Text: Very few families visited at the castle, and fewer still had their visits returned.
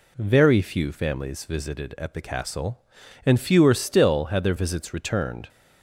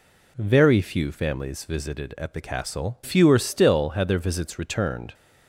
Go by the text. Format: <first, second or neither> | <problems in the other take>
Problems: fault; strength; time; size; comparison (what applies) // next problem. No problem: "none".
first | skips "and"; at 3.0 s